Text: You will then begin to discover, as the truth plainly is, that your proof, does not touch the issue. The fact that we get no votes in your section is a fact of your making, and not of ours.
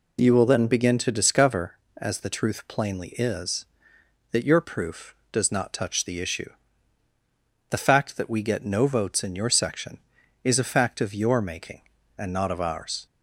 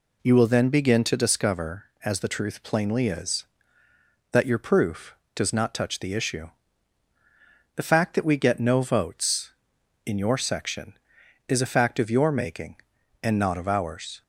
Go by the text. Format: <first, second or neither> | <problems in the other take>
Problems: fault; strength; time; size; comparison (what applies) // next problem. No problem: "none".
neither | none